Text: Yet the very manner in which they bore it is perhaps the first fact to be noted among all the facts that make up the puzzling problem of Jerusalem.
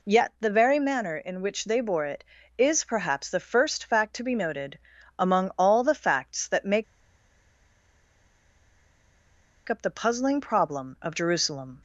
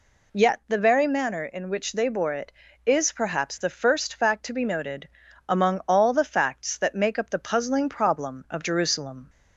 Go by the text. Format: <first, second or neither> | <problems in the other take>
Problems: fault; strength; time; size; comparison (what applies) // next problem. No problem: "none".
second | pauses between "noted" and "among"; at 4.7 s; 0.40 s long; also in the second // pauses between "make" and "up"; strong; at 6.8 s; 2.8 s long